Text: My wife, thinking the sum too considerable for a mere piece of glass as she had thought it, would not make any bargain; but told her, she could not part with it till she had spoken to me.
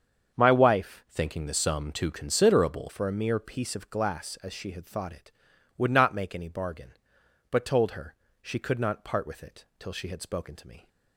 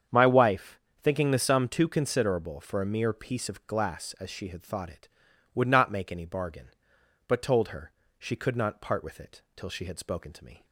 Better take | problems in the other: second | starts louder than the rest; strong; until 1.4 s; 7 dB; strong in the second // changes voice from "thinking" to "considerable"; from 1.1 to 2.8 s; 1.7 s long

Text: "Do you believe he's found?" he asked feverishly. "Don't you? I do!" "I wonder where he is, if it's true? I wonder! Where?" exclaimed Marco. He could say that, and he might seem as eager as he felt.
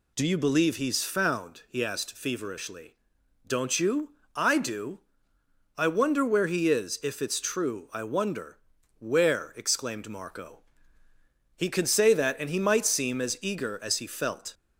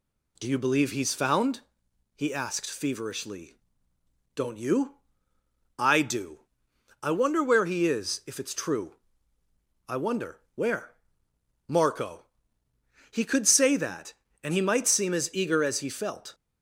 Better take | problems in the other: first | skips "exclaimed"; at 11.3 s

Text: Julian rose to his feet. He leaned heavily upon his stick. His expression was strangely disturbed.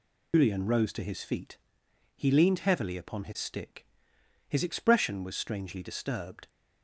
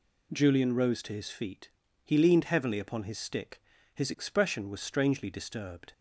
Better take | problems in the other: second | loses the start of "Julian"; at 0.3 s; 155 ms

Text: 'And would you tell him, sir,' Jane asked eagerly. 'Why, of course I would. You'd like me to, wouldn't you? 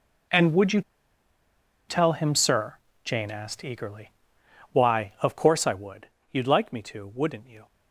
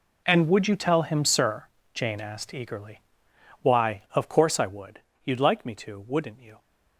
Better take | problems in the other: second | pauses between "you" and "tell"; at 0.8 s; 1.0 s long

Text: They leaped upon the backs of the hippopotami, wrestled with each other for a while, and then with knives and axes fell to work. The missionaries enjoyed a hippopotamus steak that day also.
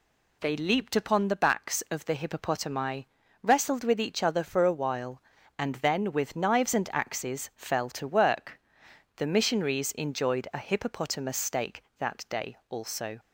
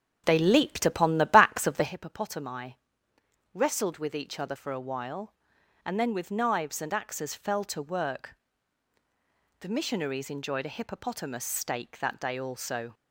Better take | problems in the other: first | starts louder than the rest; strong; until 2.0 s; 7.5 dB

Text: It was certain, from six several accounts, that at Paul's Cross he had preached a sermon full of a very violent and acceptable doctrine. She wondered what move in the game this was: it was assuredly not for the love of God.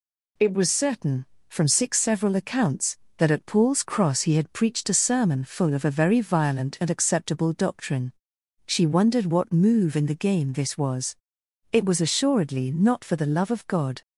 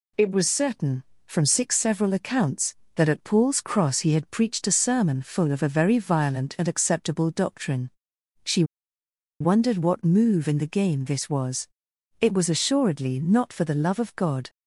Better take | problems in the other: first | pauses between "She" and "wondered"; noticeable; at 8.6 s; 0.77 s long

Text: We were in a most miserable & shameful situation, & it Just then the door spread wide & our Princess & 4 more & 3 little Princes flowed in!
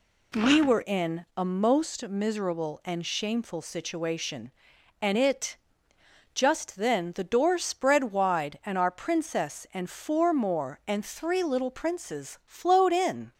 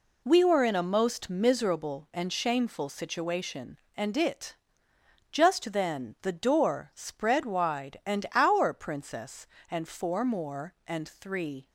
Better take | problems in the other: first | pauses between "it" and "Just"; noticeable; at 4.5 s; 0.76 s long; noticeable in the first // stops before "little Princes flowed in"; at 11.6 s

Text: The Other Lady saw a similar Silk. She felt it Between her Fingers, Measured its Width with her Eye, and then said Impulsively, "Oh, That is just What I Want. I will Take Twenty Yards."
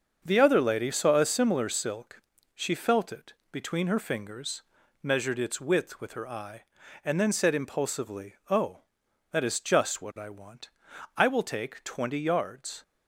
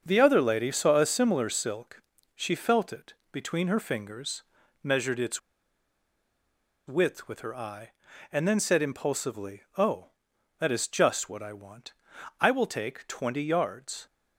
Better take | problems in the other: first | starts louder than the rest; until 1.0 s; 6.5 dB; also in the first // pauses between "it" and "Between"; slight; at 3.1 s; 0.18 s long; slight in the first // pauses between "its" and "Width"; strong; at 5.3 s; 1.4 s long

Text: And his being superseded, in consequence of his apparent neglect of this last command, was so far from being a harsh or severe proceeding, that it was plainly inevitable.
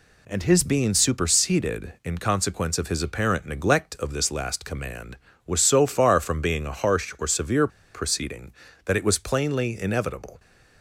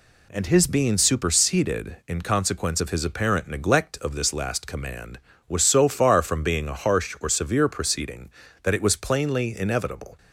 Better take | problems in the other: second | pauses between "severe" and "proceeding"; slight; at 7.6 s; 0.26 s long

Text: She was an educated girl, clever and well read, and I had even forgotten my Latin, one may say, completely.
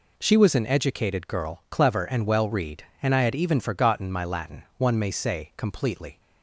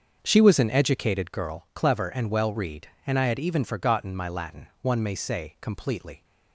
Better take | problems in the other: first | starts louder than the rest; until 1.5 s; 6.5 dB

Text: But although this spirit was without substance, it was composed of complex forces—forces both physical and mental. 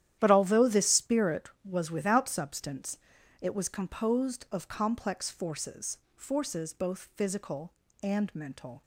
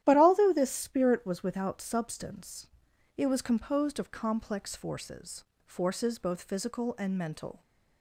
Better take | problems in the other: neither | starts louder than the rest; strong; the same in both

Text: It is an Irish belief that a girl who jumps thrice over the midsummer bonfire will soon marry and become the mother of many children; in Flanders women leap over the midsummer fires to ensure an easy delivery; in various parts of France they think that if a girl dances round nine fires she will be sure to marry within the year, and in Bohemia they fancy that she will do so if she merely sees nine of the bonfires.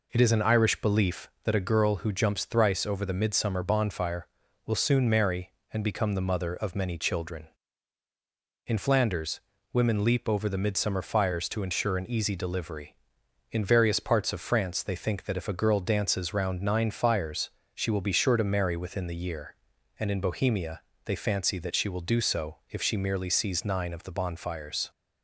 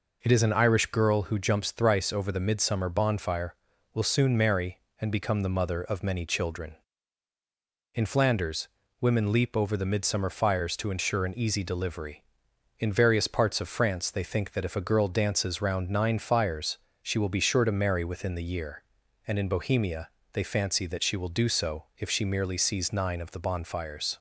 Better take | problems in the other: first | skips "belief that a"; at 0.9 s // pauses between "Flanders" and "women"; slight; at 8.6 s; 0.34 s long; slight in the first // pauses between "fires" and "she"; slight; at 16.7 s; 0.24 s long; slight in the first // pauses between "Bohemia" and "they"; slight; at 20.0 s; 0.24 s long; slight in the first

